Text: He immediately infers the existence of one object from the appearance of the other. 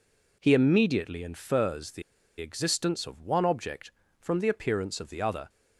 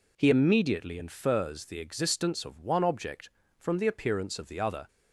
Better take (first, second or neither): second